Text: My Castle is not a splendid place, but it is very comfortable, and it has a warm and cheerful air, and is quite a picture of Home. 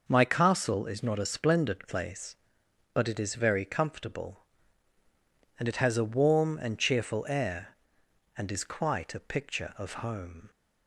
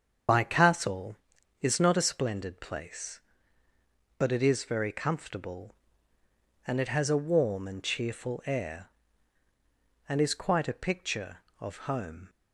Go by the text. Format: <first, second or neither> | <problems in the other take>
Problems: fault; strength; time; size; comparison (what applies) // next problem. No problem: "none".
first | loses the start of "My"; at 0.2 s; 85 ms // starts louder than the rest; strong; until 1.7 s; 7.5 dB